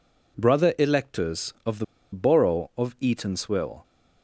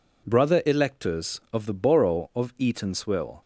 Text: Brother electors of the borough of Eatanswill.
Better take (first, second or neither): second